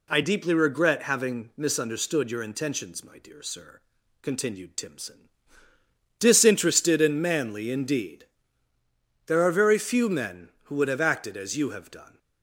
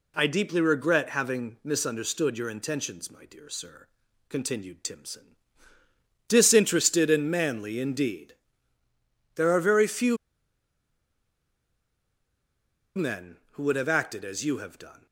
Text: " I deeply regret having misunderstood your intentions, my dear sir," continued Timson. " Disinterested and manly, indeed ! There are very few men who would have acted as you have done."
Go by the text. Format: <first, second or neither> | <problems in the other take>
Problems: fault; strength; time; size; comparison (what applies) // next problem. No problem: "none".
first | pauses between "few" and "men"; strong; at 10.1 s; 2.7 s long